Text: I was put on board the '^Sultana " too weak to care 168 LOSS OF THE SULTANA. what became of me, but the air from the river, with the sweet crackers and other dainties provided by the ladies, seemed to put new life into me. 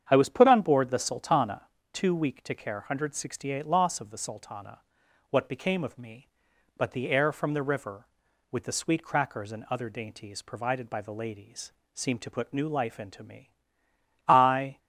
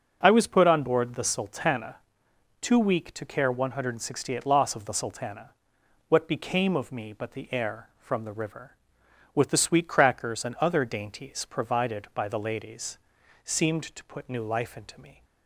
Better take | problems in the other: second | starts louder than the rest; strong; until 1.0 s; 8.5 dB; strong in the second // goes on to say "I"; from 14.2 s on; 0.50 s long

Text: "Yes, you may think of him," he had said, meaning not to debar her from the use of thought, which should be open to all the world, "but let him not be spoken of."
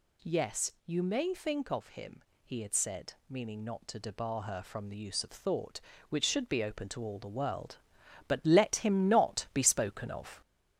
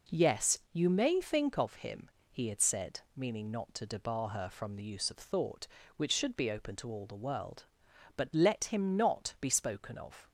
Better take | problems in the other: second | gets louder; noticeable; throughout; 4 dB

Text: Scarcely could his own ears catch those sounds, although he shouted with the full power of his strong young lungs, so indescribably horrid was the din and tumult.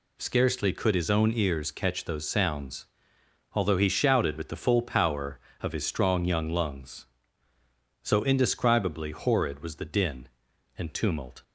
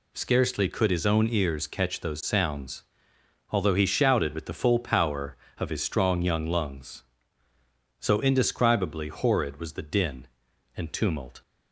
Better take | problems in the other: neither | none

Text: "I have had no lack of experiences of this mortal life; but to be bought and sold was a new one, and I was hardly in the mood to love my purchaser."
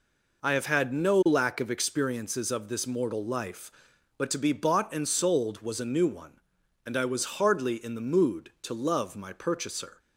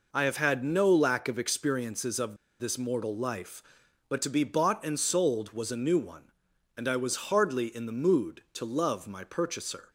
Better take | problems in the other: first | pauses between "of" and "this"; slight; at 2.3 s; 0.25 s long

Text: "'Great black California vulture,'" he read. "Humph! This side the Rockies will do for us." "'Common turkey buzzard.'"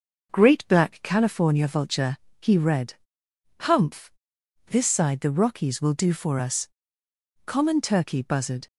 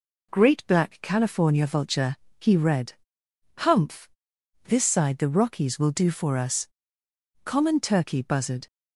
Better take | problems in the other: second | starts louder than the rest; noticeable; until 1.5 s; 6 dB

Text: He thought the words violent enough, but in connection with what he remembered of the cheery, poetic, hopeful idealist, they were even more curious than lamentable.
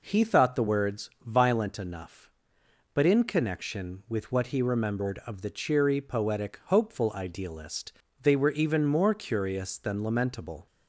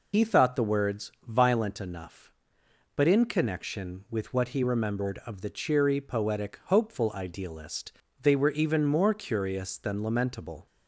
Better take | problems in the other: first | loses the start of "He"; at 0.1 s; 90 ms

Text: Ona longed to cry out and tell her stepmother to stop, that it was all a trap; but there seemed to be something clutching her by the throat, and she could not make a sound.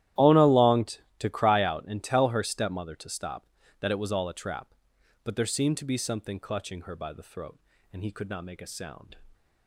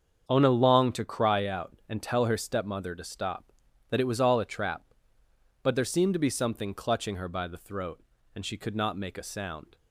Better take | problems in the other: second | starts louder than the rest; strong; until 1.3 s; 13 dB; strong in the second // says "he" for "she"; at 8.0 s

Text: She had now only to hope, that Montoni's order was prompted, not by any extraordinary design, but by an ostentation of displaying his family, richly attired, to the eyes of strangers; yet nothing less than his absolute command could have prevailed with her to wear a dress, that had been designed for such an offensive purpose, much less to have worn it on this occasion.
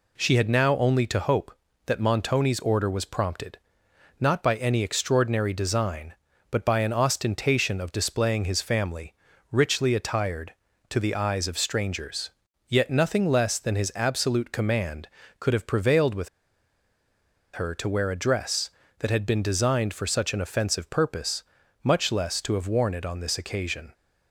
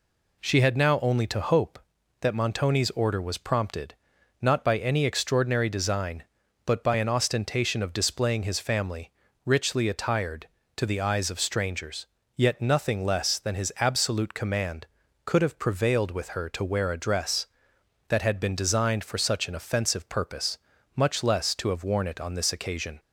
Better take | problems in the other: second | pauses between "with" and "her"; strong; at 16.2 s; 1.2 s long

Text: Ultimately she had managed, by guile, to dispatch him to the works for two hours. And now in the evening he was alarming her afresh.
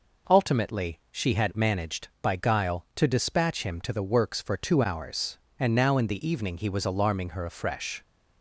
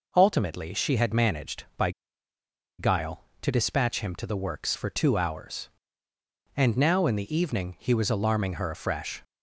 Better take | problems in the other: first | pauses between "by" and "guile"; noticeable; at 1.9 s; 0.88 s long

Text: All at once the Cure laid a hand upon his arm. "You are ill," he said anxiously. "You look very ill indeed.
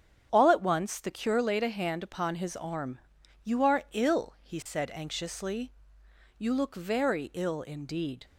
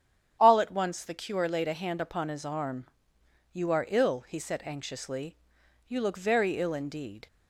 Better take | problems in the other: neither | starts louder than the rest; strong; the same in both

